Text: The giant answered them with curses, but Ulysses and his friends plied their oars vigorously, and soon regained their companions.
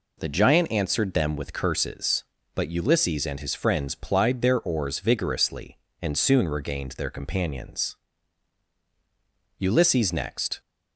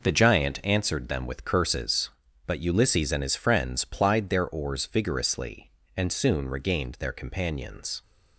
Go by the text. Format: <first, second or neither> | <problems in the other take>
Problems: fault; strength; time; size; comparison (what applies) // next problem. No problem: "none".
second | goes on to say "Ulysses next"; noticeable; from 9.5 s on; 1.0 s long